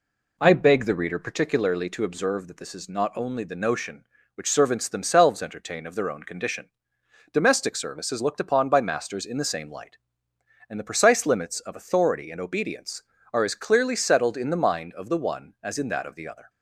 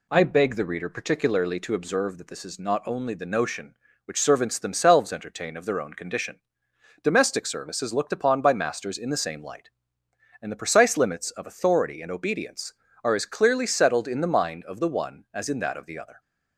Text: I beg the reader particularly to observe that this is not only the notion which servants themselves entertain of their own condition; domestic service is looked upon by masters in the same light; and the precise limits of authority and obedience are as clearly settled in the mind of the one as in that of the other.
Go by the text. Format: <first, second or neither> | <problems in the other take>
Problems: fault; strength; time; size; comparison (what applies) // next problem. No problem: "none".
second | starts louder than the rest; slight; until 1.4 s; 3 dB